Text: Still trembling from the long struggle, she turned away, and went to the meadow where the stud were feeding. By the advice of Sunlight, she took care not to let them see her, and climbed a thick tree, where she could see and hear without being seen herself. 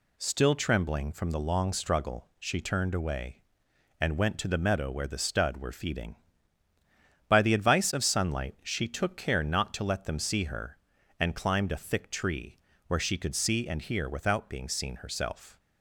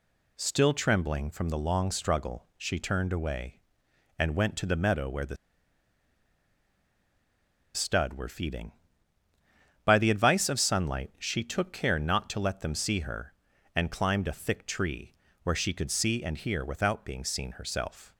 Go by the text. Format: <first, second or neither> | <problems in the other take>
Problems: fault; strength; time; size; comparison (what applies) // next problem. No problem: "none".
first | pauses between "the" and "stud"; strong; at 5.3 s; 2.3 s long